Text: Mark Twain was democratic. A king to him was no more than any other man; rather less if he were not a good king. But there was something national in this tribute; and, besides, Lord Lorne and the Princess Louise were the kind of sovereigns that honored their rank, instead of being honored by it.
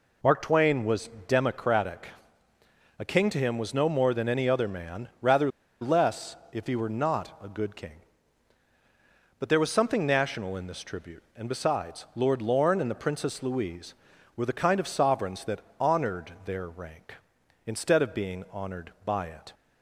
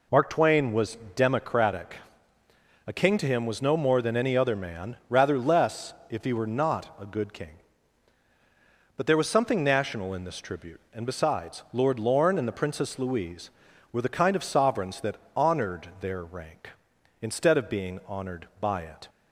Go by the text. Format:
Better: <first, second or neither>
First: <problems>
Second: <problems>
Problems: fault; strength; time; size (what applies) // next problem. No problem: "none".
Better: second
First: pauses between "was" and "democratic"; slight; at 1.0 s; 0.18 s long // pauses between "rather" and "less"; slight; at 5.4 s; 0.32 s long // pauses between "less" and "if"; slight; at 6.3 s; 0.16 s long // pauses between "that" and "honored"; slight; at 15.6 s; 0.18 s long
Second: pauses between "was" and "democratic"; slight; at 0.9 s; 0.18 s long // pauses between "less" and "if"; slight; at 5.9 s; 0.16 s long // pauses between "that" and "honored"; slight; at 15.1 s; 0.18 s long